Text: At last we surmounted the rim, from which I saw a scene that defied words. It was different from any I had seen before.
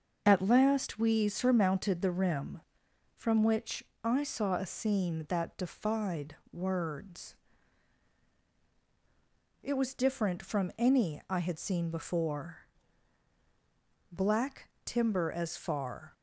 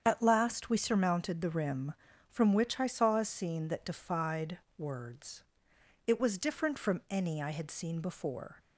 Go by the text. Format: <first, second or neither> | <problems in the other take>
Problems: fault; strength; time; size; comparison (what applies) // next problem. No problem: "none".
second | starts louder than the rest; until 1.2 s; 6.5 dB; strong in the second // pauses between "which" and "I"; slight; at 3.8 s; 0.22 s long // pauses between "defied" and "words"; slight; at 6.3 s; 0.16 s long; slight in the second // goes on to say "Black timber as far"; strong; from 14.1 s on; 2.0 s long